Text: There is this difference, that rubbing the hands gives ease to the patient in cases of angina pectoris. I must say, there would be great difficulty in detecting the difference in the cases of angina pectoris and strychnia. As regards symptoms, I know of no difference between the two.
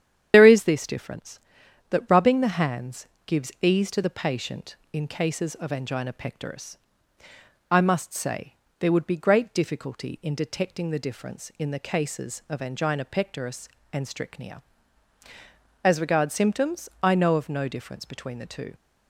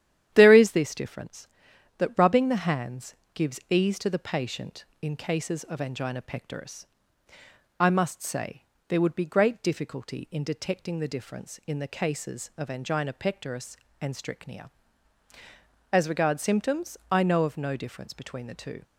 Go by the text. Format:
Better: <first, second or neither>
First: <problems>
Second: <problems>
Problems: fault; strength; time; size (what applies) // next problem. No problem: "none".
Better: second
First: loses the start of "There"; at 0.3 s; 75 ms // starts louder than the rest; strong; until 1.3 s; 9.5 dB // pauses between "hands" and "gives"; slight; at 3.0 s; 0.20 s long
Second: starts louder than the rest; strong; until 1.3 s; 10.5 dB // pauses between "hands" and "gives"; slight; at 3.1 s; 0.20 s long